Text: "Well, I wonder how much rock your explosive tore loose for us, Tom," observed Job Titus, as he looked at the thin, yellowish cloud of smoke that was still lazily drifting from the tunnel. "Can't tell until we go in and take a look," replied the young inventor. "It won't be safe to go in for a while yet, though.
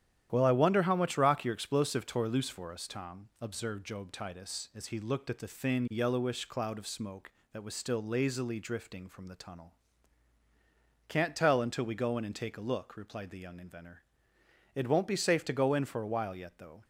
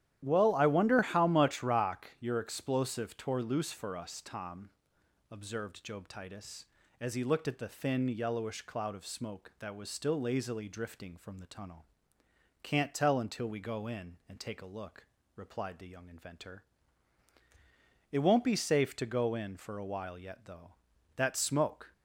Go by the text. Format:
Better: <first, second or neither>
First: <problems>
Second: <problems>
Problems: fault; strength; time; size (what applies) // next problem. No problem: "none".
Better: first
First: starts louder than the rest; strong; until 1.3 s; 11 dB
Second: starts louder than the rest; strong; until 1.2 s; 12 dB // goes on to say "That smoke"; noticeable; from 21.1 s on; 0.76 s long